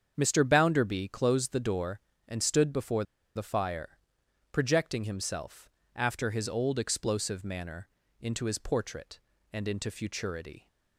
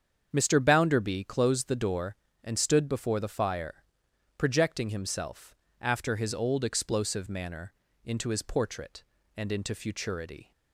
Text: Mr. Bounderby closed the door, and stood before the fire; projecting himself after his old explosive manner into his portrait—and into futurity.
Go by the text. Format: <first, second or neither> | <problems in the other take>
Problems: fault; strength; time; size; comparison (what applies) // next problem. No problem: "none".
second | starts louder than the rest; strong; until 1.1 s; 7.5 dB; strong in the second // pauses between "before" and "the"; slight; at 3.0 s; 0.30 s long // pauses between "himself" and "after"; slight; at 5.6 s; 0.26 s long; slight in the second // pauses between "manner" and "into"; slight; at 7.8 s; 0.32 s long; slight in the second